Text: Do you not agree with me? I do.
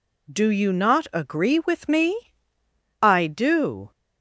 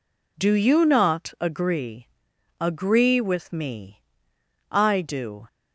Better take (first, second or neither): first